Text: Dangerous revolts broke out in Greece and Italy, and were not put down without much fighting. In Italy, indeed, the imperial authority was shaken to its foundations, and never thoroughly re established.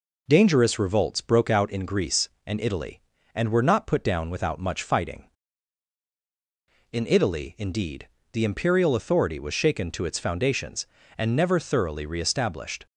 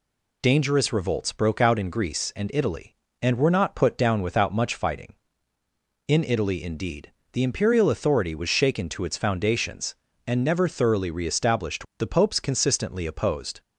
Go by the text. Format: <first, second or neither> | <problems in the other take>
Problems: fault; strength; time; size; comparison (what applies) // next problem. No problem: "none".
first | goes on to say "The Popes consistently opposed"; from 11.9 s on; 1.6 s long